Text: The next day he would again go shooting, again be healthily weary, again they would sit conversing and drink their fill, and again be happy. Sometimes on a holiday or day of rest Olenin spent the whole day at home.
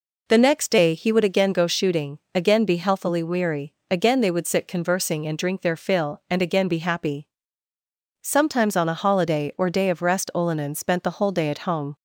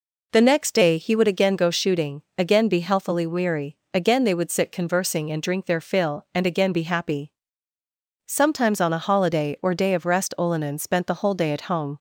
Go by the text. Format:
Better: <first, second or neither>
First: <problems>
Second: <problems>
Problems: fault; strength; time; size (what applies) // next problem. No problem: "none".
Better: neither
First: none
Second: none